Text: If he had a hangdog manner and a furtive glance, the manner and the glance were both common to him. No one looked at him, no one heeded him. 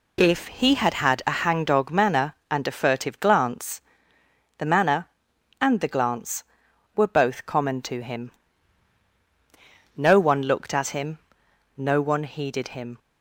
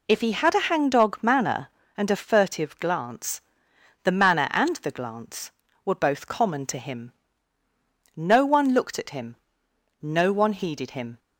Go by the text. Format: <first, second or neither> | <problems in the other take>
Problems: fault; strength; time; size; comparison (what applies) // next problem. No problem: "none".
second | says "had" twice; at 0.9 s